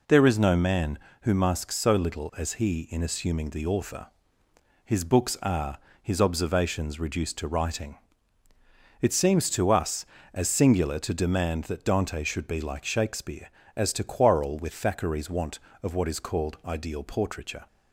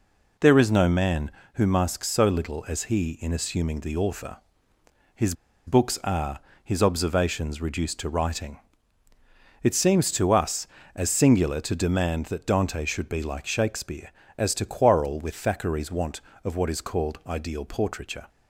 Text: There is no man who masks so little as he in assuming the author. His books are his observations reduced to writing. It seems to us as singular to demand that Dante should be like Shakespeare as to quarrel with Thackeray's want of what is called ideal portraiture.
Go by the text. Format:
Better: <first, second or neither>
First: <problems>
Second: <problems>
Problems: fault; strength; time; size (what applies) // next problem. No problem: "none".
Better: first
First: pauses between "are" and "his"; slight; at 5.7 s; 0.22 s long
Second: pauses between "His" and "books"; slight; at 5.3 s; 0.33 s long // pauses between "are" and "his"; slight; at 6.4 s; 0.22 s long